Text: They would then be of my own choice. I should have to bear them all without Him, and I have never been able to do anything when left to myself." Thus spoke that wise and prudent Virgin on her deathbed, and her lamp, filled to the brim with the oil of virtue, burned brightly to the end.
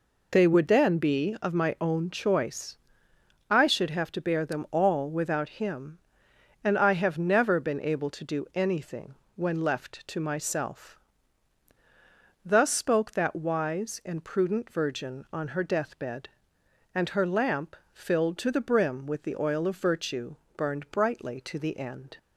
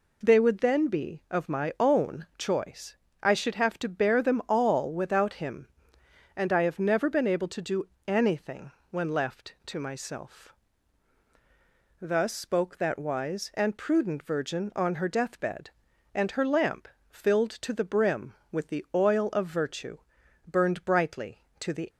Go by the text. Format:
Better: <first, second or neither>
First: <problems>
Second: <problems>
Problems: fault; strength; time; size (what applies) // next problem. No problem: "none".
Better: first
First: pauses between "anything" and "when"; slight; at 9.1 s; 0.22 s long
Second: pauses between "do" and "anything"; slight; at 7.8 s; 0.20 s long // pauses between "anything" and "when"; slight; at 8.7 s; 0.20 s long // stops before "end"; at 21.9 s